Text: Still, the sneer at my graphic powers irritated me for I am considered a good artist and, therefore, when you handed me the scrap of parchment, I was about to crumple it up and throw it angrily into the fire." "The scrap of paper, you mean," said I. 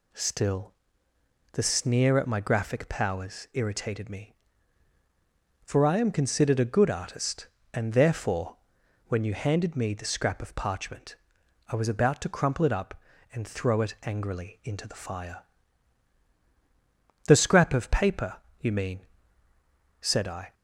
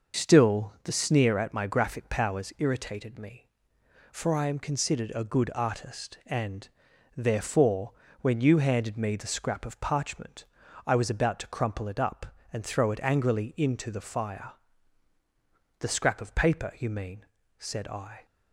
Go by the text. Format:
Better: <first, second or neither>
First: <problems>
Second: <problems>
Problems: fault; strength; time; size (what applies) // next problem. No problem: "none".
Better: first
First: none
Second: loses the start of "Still"; at 0.1 s; 65 ms